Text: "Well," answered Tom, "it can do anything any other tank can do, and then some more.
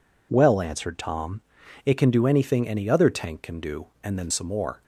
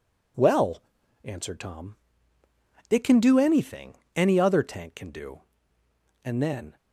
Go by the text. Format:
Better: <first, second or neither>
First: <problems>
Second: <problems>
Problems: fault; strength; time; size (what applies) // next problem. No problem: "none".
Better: first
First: none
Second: pauses between "anything" and "any"; slight; at 3.9 s; 0.22 s long // stops before "some more"; at 6.7 s